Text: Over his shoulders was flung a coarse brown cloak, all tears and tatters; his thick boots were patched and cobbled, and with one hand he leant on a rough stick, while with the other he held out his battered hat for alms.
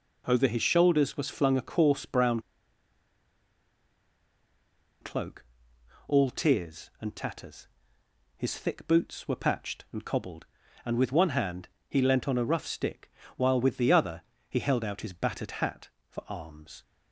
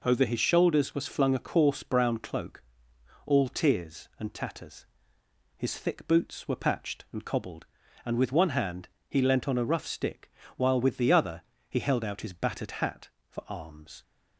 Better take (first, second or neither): second